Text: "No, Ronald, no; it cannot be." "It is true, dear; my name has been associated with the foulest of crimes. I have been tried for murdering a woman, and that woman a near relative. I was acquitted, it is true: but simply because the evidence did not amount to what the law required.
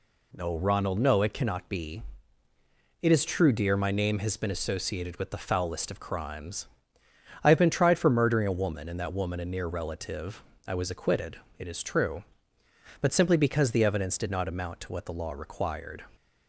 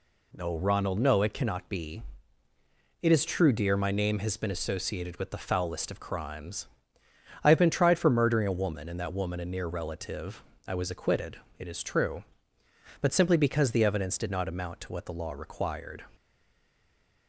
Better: first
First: none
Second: stays silent after the last word; from 16.1 s on; 1.1 s long

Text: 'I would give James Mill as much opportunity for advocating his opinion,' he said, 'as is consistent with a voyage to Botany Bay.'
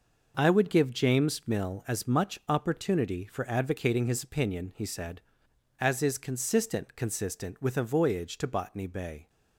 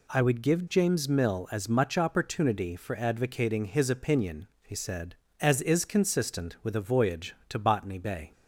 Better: second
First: says "consistent" twice; at 6.9 s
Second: none

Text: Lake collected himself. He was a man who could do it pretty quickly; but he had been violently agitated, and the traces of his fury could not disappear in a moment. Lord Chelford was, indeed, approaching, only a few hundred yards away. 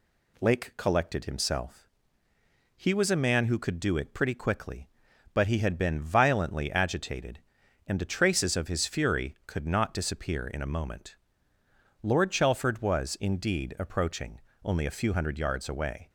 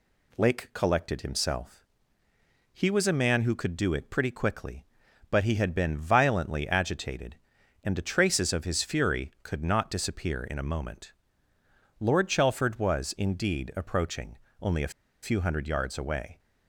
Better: first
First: none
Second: pauses between "a" and "few"; slight; at 14.9 s; 0.32 s long

